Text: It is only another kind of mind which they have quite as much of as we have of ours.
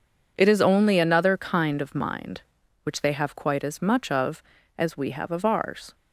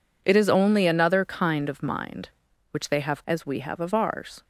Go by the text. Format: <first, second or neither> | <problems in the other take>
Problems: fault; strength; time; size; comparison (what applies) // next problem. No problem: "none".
first | skips "quite as much of"; at 3.2 s